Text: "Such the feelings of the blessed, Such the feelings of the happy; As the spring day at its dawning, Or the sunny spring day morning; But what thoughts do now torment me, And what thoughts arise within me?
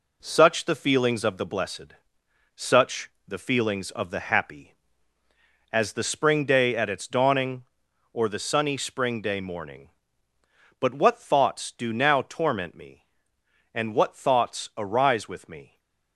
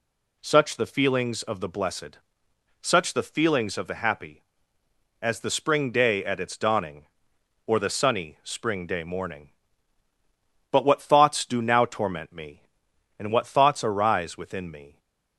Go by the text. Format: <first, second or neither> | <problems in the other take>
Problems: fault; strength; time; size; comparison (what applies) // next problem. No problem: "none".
second | pauses between "Such" and "the"; slight; at 3.0 s; 0.18 s long // says "with" for "within"; at 15.2 s // stays silent after the last word; slight; from 15.6 s on; 0.5 s long